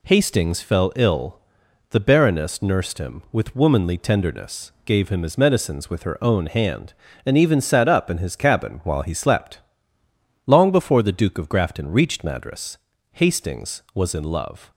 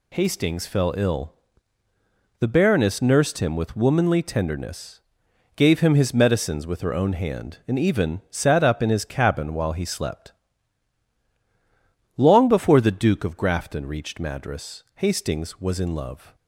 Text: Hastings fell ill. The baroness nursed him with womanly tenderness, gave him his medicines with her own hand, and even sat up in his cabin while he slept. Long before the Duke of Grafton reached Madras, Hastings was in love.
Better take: neither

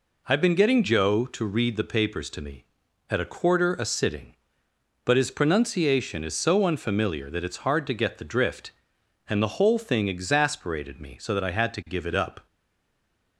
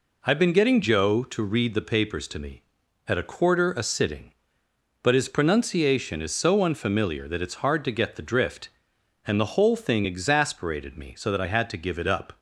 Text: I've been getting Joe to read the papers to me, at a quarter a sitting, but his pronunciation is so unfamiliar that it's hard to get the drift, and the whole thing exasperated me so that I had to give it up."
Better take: second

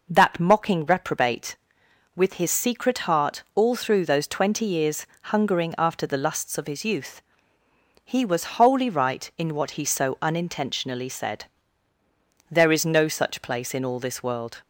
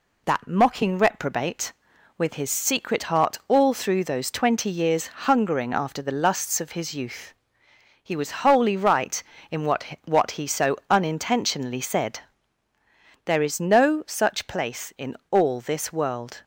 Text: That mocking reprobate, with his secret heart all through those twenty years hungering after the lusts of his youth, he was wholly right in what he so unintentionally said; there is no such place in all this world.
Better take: first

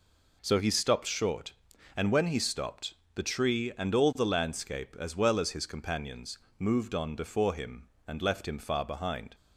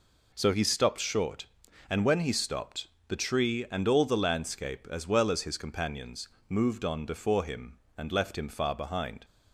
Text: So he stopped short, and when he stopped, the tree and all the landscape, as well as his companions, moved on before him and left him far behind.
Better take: neither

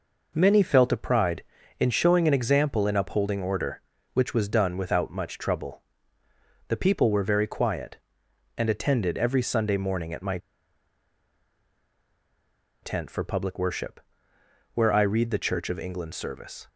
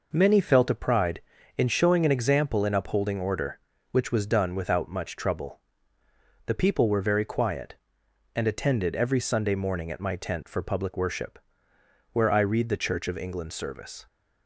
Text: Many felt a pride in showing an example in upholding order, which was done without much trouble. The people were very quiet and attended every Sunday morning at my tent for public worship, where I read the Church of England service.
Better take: second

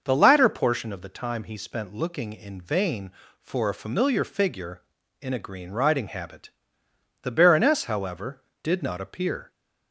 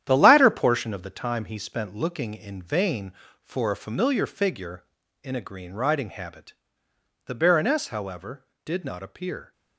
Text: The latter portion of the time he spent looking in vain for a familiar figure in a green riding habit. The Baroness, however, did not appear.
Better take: first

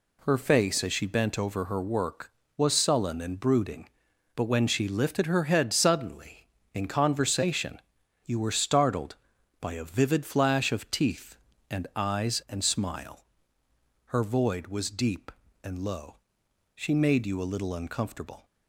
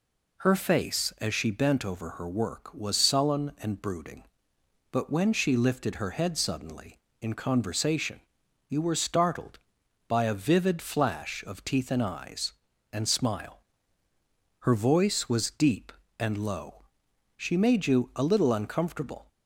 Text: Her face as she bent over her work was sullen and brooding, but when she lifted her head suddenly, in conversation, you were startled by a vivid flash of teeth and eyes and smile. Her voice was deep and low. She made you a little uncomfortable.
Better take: second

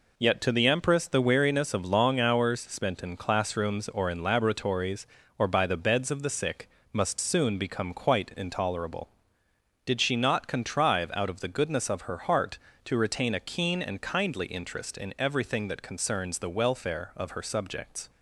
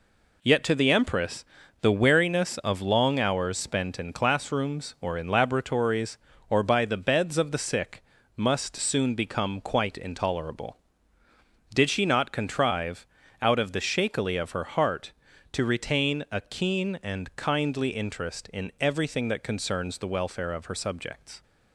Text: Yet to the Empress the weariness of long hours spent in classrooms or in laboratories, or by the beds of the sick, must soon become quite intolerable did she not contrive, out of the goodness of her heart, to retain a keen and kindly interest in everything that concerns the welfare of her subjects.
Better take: first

